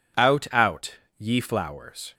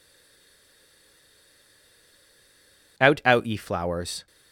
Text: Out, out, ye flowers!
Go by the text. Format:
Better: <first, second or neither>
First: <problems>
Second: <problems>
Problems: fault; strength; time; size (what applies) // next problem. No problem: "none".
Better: first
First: none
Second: stays silent before the first word; strong; until 2.9 s; 2.9 s long